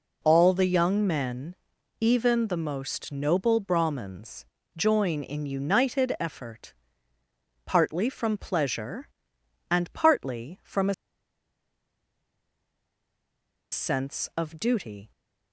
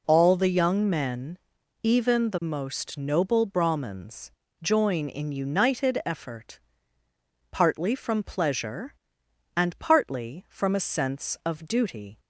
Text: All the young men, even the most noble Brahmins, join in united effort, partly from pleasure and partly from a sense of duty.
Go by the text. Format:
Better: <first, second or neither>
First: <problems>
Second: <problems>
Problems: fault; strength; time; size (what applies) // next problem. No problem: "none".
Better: second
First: pauses between "a" and "sense"; strong; at 10.9 s; 2.7 s long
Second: none